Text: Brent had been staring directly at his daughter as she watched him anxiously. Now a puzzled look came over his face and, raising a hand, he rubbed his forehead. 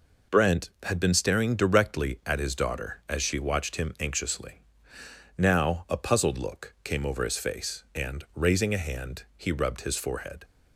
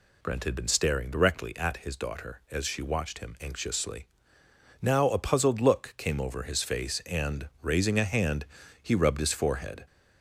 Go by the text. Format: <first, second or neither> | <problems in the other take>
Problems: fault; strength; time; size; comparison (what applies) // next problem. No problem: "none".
neither | none